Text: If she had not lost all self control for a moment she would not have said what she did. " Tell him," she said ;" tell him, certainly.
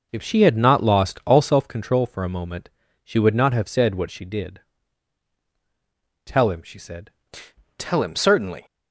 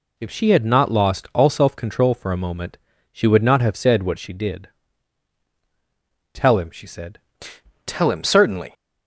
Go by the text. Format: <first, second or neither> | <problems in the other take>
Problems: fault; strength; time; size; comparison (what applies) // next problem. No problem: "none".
second | starts louder than the rest; until 1.7 s; 7 dB // pauses between "moment" and "she"; slight; at 2.6 s; 0.34 s long; slight in the second